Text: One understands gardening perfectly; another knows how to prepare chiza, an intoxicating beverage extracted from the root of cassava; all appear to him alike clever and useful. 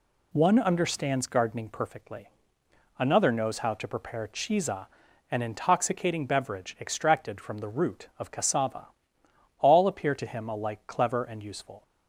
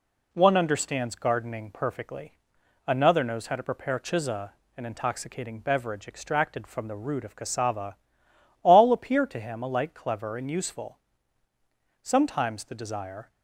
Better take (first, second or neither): first